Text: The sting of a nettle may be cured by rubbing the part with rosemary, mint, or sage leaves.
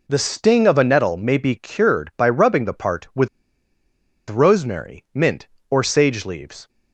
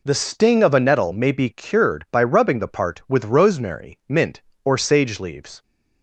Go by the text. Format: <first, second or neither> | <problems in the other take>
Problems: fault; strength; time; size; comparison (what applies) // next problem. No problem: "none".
second | pauses between "with" and "rosemary"; at 3.2 s; 1.0 s long